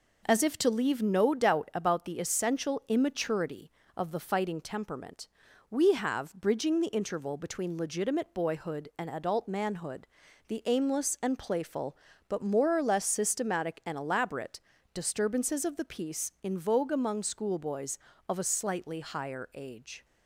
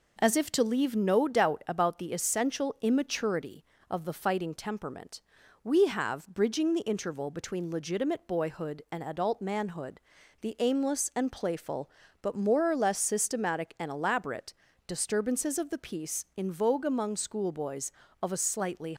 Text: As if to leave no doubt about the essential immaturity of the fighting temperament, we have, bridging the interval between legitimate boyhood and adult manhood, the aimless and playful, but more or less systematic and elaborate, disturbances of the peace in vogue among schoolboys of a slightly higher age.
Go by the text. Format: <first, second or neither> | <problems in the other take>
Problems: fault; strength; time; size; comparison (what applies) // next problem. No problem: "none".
first | stops before "higher age"; at 18.9 s